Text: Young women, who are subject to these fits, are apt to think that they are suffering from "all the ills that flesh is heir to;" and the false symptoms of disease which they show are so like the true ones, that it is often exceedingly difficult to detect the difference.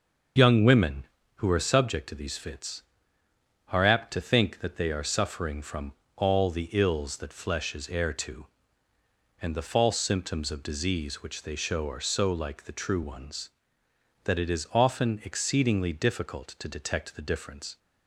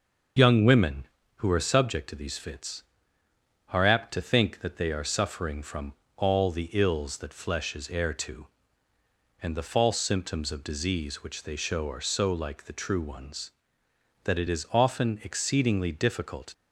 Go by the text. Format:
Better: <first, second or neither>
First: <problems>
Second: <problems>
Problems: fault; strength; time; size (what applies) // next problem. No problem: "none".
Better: first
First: starts louder than the rest; noticeable; until 1.6 s; 6 dB // pauses between "from" and "all"; slight; at 5.9 s; 0.22 s long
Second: starts louder than the rest; noticeable; until 1.6 s; 6 dB // pauses between "from" and "all"; slight; at 5.9 s; 0.22 s long // stops before "to detect the difference"; at 16.5 s